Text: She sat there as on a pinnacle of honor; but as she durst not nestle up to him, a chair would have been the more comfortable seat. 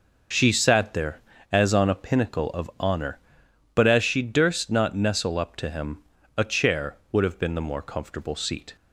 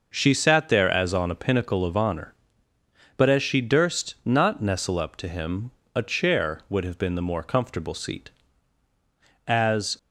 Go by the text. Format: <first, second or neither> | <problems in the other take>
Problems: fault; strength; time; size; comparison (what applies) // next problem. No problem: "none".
first | goes on to say "As"; from 9.4 s on; 0.50 s long